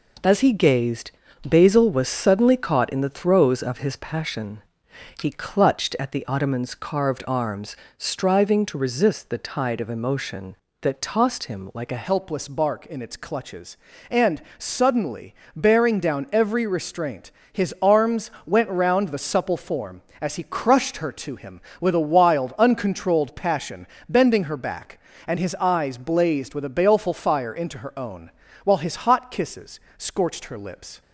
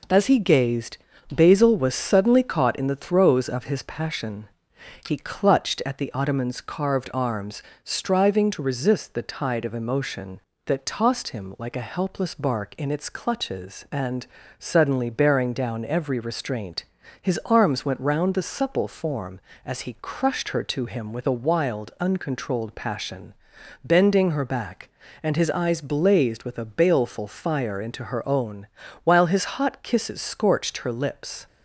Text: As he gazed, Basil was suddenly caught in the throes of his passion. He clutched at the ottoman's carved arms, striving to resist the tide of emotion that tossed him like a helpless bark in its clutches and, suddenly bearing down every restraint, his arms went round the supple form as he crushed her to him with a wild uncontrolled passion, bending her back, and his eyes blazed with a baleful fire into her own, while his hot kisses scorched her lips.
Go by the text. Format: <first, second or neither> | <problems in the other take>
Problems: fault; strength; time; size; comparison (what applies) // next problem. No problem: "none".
second | changes voice at "helpless"; from 12.0 s on; 19.0 s long // pauses between "suddenly" and "bearing"; slight; at 15.3 s; 0.22 s long // pauses between "arms" and "went"; slight; at 18.2 s; 0.16 s long // pauses between "kisses" and "scorched"; slight; at 29.7 s; 0.18 s long